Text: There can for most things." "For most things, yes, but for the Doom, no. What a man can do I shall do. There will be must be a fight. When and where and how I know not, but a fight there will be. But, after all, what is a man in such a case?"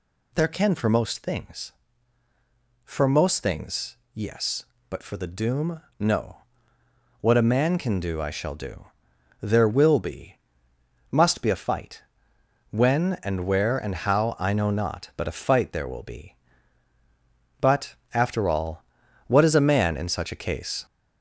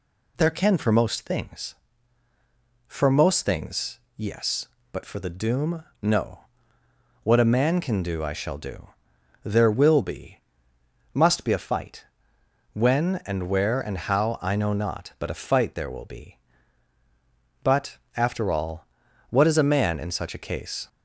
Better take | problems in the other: second | gets louder; slight; throughout; 3 dB // pauses between "be" and "must"; noticeable; at 10.3 s; 0.76 s long; noticeable in the second

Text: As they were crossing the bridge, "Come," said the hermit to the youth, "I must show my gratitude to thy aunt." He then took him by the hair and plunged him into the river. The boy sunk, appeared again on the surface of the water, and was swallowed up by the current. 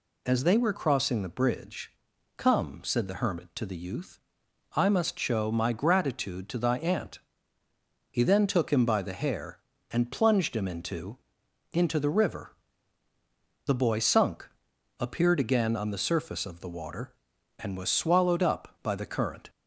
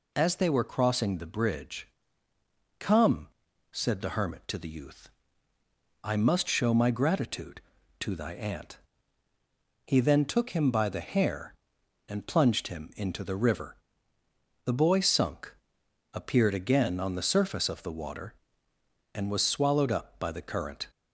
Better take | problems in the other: second | says "into" twice; at 11.7 s

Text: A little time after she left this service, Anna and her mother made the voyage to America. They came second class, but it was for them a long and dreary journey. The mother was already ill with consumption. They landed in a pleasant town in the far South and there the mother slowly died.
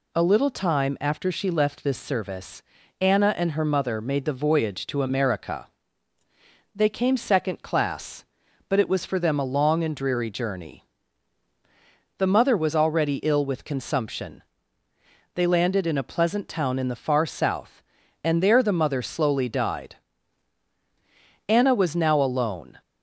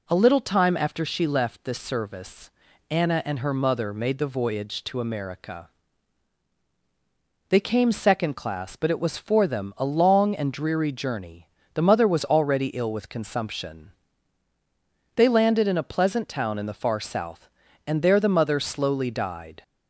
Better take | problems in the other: second | goes on to say "Anna was now alone"; from 21.4 s on; 1.3 s long

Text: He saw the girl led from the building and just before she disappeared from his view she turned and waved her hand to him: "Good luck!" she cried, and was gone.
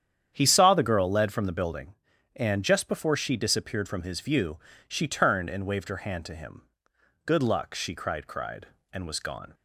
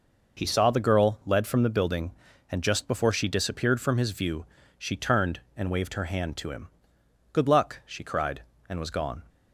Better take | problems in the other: second | starts louder than the rest; strong; until 1.3 s; 9 dB // pauses between "view" and "she"; slight; at 4.5 s; 0.30 s long; slight in the second // says "cried" twice; at 8.2 s

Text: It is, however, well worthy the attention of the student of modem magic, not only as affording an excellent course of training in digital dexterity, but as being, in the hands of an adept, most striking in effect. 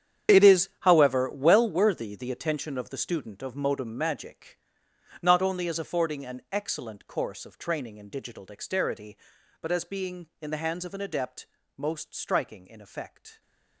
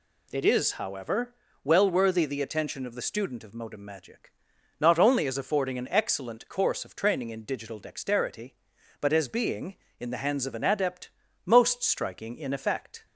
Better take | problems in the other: second | gets quieter; strong; throughout; 15 dB

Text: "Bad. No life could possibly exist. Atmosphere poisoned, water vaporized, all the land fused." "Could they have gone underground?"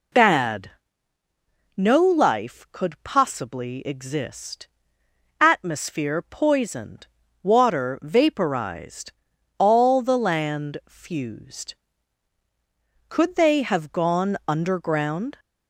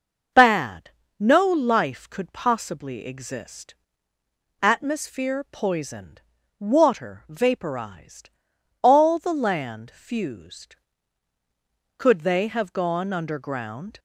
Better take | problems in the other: neither | none

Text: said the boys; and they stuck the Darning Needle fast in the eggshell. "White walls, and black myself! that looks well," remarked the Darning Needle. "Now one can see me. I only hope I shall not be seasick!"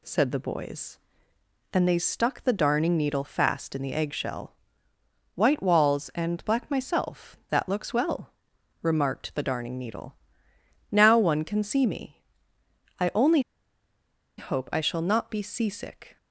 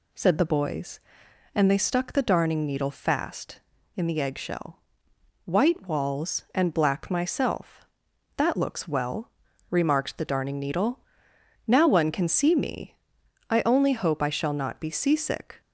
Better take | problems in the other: second | pauses between "only" and "hope"; at 13.3 s; 0.98 s long

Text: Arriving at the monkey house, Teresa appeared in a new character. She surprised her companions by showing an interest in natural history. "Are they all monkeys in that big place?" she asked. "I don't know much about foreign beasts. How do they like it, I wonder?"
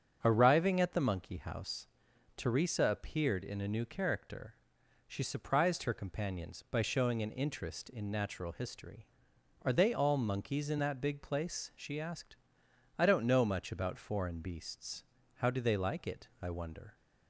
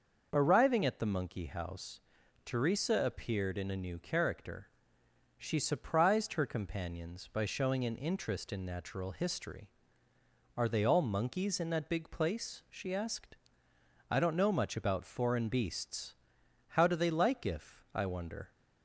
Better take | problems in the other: first | starts louder than the rest; noticeable; until 1.3 s; 6 dB; strong in the first // says "if" for "it"; at 17.4 s

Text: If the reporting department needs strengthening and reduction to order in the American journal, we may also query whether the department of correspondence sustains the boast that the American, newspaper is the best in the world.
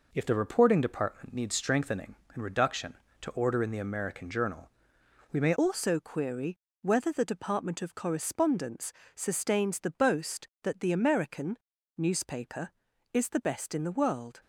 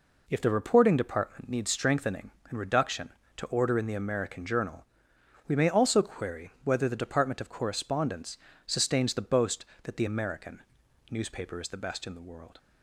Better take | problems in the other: second | changes voice at "also"; from 5.5 s on; 8.9 s long // pauses between "query" and "whether"; slight; at 6.5 s; 0.24 s long // pauses between "correspondence" and "sustains"; slight; at 8.9 s; 0.24 s long; slight in the second

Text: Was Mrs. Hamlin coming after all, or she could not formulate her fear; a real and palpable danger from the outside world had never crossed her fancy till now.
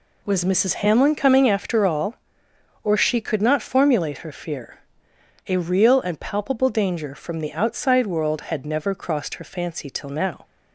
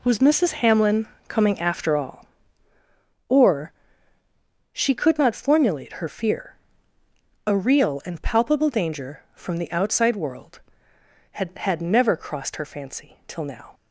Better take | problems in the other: first | pauses between "Hamlin" and "coming"; slight; at 1.0 s; 0.22 s long // pauses between "or" and "she"; at 3.7 s; 1.0 s long // says "had" twice; at 11.5 s

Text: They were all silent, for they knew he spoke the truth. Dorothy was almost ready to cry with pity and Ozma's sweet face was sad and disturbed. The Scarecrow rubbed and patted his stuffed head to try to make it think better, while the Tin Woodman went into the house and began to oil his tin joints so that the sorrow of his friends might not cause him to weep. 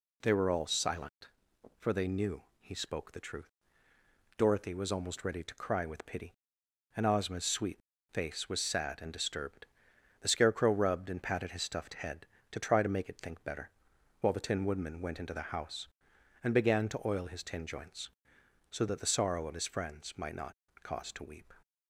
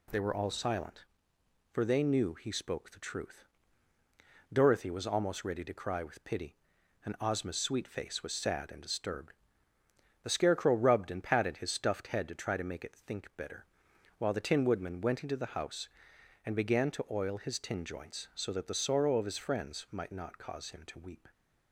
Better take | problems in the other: second | pauses between "knew" and "he"; slight; at 2.4 s; 0.18 s long // pauses between "sweet" and "face"; slight; at 7.7 s; 0.34 s long // pauses between "not" and "cause"; slight; at 20.5 s; 0.26 s long // skips "him"; at 21.1 s

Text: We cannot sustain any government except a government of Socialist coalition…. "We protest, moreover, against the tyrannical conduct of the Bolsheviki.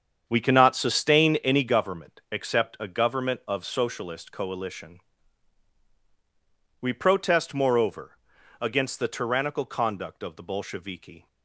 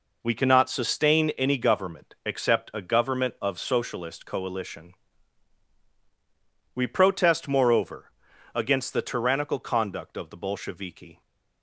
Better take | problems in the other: second | starts louder than the rest; strong; until 1.8 s; 7.5 dB

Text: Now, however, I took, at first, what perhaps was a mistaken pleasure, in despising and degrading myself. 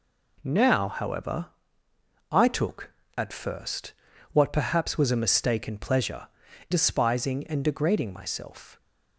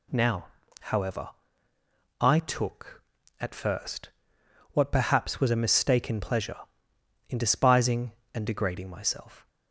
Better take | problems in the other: second | skips "in"; at 6.4 s

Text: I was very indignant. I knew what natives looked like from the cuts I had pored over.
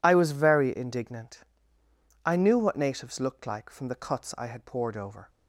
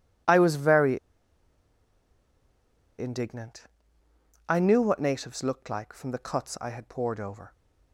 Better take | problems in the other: first | pauses between "very" and "indignant"; strong; at 0.9 s; 1.9 s long

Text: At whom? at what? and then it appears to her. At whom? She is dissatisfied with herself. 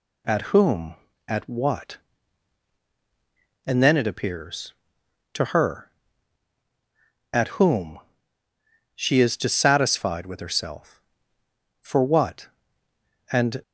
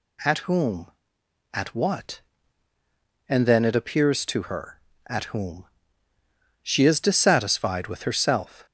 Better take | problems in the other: second | goes on to say "For what And"; strong; from 11.7 s on; 1.8 s long

